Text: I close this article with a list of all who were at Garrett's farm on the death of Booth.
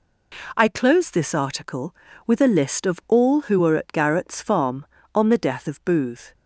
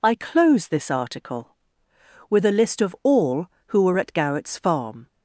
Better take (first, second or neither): first